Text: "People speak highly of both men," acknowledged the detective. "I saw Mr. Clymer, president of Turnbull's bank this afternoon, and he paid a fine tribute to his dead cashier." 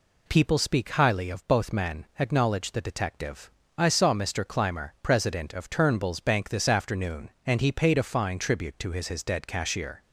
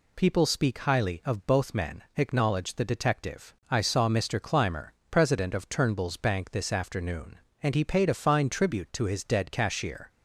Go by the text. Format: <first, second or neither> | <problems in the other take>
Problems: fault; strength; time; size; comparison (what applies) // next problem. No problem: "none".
second | says "his" twice; at 9.0 s